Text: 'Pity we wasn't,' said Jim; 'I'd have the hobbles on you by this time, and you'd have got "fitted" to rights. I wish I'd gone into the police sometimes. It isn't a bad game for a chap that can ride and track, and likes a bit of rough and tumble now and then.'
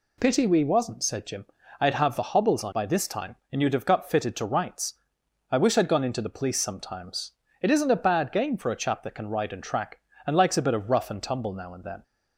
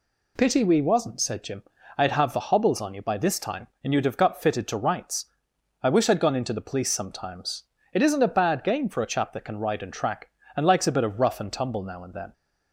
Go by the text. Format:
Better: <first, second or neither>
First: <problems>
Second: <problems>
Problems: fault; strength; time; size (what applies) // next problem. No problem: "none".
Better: second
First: skips "you"; at 2.7 s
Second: none